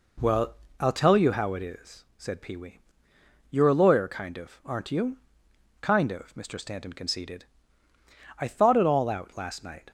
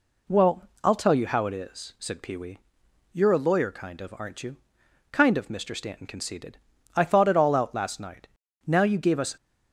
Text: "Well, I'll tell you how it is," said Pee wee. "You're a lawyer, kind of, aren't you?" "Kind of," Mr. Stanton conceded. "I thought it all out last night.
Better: first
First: none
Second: goes on to say "Now you gave us"; noticeable; from 8.6 s on; 0.70 s long

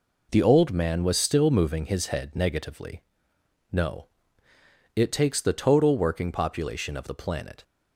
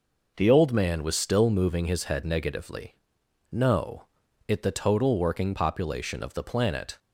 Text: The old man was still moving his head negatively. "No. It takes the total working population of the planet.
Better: first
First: none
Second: skips "takes"; at 4.6 s

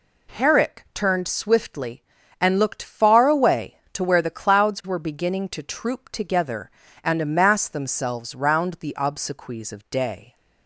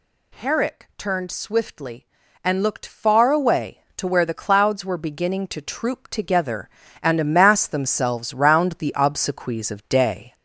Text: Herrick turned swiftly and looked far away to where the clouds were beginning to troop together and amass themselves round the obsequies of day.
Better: first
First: none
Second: gets louder; noticeable; throughout; 4 dB

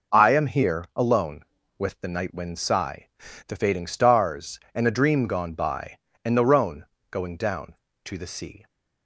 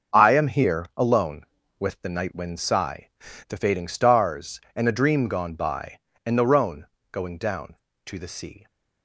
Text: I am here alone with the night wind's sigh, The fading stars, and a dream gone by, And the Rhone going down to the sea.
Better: first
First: pauses between "Rhone" and "going"; slight; at 6.8 s; 0.26 s long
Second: gets quieter; strong; throughout; 9.5 dB // pauses between "Rhone" and "going"; slight; at 6.8 s; 0.26 s long

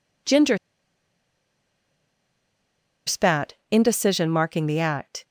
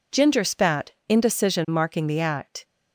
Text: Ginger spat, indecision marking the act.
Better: second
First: pauses between "Ginger" and "spat"; strong; at 0.5 s; 2.4 s long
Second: none

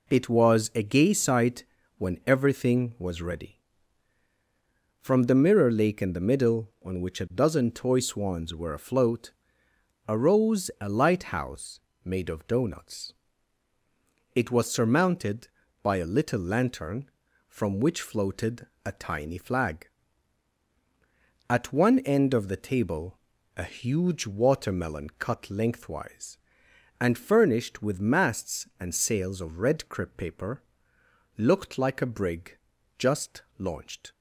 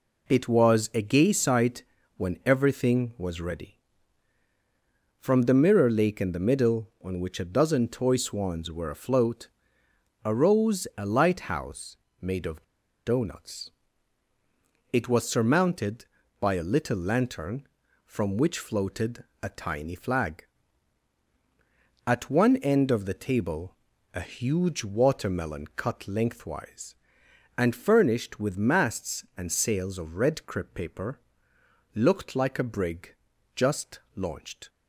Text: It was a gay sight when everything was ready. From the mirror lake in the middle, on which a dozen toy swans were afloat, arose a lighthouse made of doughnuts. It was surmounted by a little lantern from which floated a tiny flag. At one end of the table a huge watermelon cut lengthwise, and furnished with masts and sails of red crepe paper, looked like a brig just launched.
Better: first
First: pauses between "sight" and "when"; slight; at 1.6 s; 0.32 s long // pauses between "lighthouse" and "made"; slight; at 11.7 s; 0.24 s long // pauses between "floated" and "a"; slight; at 18.6 s; 0.18 s long // pauses between "table" and "a"; slight; at 23.1 s; 0.36 s long // pauses between "brig" and "just"; at 32.5 s; 0.40 s long // pauses between "just" and "launched"; slight; at 33.4 s; 0.16 s long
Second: pauses between "sight" and "when"; slight; at 1.8 s; 0.32 s long // pauses between "lighthouse" and "made"; slight; at 11.9 s; 0.24 s long // pauses between "of" and "doughnuts"; at 12.6 s; 0.41 s long // pauses between "floated" and "a"; slight; at 19.2 s; 0.18 s long // pauses between "table" and "a"; slight; at 23.7 s; 0.36 s long // pauses between "brig" and "just"; at 33.1 s; 0.40 s long // pauses between "just" and "launched"; slight; at 33.9 s; 0.16 s long

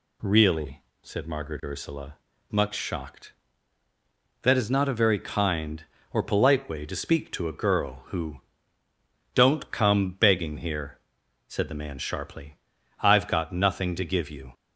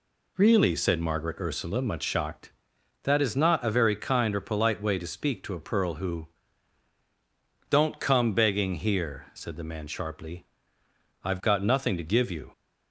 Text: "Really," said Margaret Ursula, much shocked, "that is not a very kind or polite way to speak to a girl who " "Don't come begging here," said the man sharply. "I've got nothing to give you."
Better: first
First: none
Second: says "pearl" for "girl"; at 5.5 s

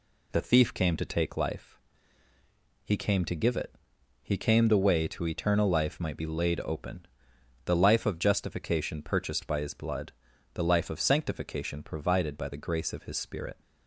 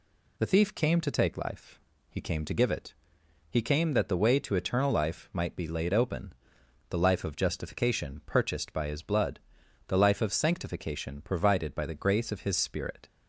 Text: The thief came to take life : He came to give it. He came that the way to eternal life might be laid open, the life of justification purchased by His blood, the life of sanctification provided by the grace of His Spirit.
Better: second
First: skips "that"; at 4.6 s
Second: none

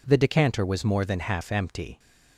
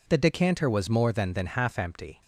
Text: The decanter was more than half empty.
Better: first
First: none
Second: says "than" twice; at 1.3 s

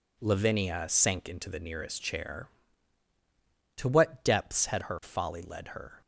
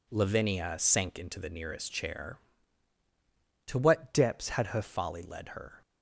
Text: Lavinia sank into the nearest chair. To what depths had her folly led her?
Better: first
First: none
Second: changes voice from "depths" to "her"; from 4.1 to 4.8 s; 0.7 s long

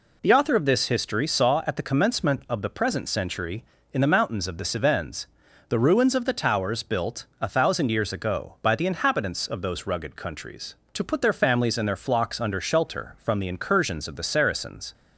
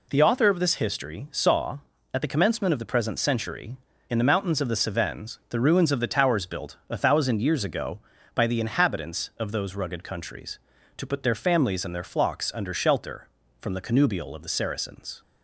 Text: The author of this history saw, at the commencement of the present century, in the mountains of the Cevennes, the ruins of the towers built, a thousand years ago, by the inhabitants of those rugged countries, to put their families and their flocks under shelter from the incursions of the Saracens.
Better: first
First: none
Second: says "connubial" for "incursions"; at 13.8 s

